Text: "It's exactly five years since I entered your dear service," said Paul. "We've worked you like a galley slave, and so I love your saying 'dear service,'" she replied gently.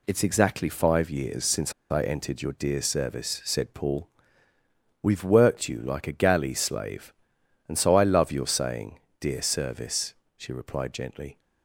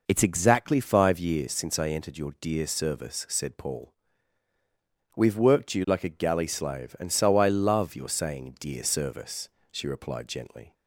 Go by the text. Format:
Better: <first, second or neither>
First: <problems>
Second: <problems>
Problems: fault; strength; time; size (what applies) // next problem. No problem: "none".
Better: second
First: pauses between "since" and "I"; slight; at 1.7 s; 0.18 s long // pauses between "saying" and "dear"; slight; at 8.9 s; 0.20 s long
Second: none